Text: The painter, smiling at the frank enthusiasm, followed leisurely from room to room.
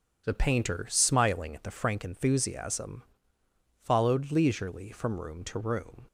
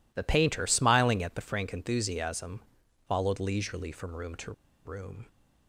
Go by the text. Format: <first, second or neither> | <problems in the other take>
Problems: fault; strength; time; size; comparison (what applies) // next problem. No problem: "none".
first | pauses between "to" and "room"; slight; at 4.5 s; 0.33 s long